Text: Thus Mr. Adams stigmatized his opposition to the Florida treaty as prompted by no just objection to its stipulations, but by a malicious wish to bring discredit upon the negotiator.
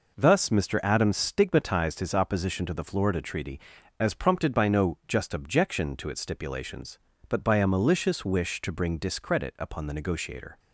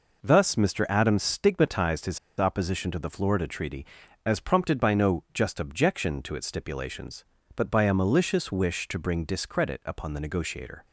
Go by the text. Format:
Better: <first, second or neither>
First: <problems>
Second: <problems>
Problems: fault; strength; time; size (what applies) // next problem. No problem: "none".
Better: first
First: none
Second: pauses between "his" and "opposition"; slight; at 2.1 s; 0.21 s long